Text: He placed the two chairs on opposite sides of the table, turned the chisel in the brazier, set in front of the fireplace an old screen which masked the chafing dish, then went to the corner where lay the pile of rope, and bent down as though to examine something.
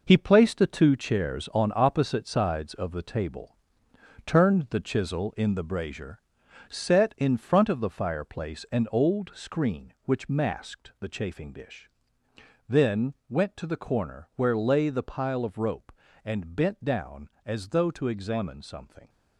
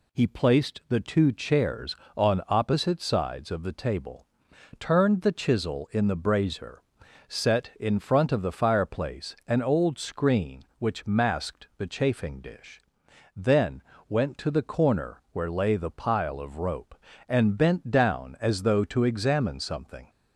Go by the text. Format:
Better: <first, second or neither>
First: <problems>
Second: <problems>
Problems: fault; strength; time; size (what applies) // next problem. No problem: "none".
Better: second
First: gets quieter; strong; throughout; 8 dB // pauses between "then" and "went"; slight; at 13.1 s; 0.16 s long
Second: pauses between "then" and "went"; slight; at 13.8 s; 0.26 s long